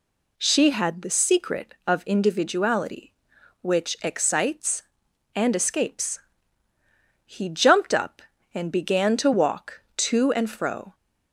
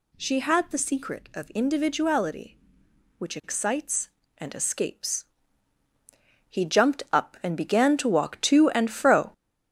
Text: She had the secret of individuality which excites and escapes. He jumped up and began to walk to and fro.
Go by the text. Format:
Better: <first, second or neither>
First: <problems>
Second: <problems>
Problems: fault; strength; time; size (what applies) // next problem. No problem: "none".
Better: first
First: none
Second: gets louder; noticeable; throughout; 5.5 dB